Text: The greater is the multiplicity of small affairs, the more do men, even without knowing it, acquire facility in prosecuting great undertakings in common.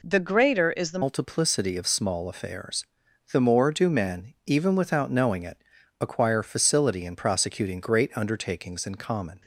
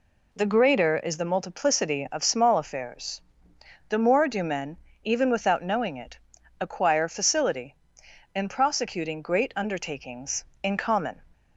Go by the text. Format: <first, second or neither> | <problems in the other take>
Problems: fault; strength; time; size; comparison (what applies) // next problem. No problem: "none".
second | changes voice at "multiplicity"; from 1.0 s on; 8.4 s long